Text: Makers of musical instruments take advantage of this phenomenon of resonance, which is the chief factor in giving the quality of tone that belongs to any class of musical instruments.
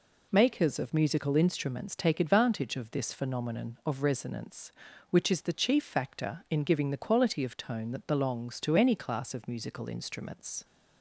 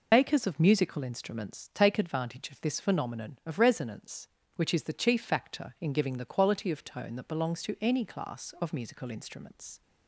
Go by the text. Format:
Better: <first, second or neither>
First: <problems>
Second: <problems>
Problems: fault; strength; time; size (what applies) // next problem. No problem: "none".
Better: first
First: none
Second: loses the start of "Makers"; at 0.1 s; 75 ms